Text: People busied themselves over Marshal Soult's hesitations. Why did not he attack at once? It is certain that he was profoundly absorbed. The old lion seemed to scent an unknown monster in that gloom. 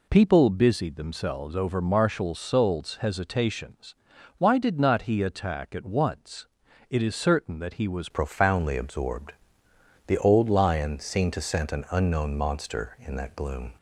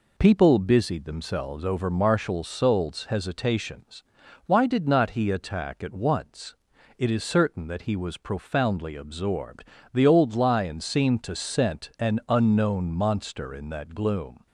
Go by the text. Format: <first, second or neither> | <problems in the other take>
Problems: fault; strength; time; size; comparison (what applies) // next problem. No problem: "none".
second | changes voice at "profoundly"; from 8.1 s on; 5.6 s long